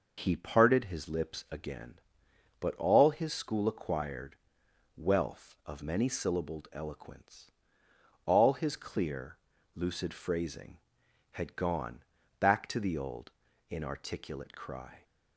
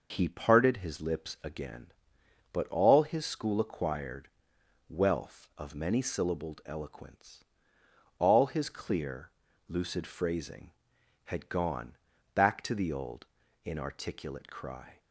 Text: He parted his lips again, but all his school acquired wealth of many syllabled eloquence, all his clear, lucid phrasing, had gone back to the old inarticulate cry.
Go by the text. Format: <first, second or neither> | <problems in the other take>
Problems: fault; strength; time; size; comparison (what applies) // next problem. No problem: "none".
neither | pauses between "acquired" and "wealth"; noticeable; the same in both // pauses between "gone" and "back"; the same in both // pauses between "old" and "inarticulate"; the same in both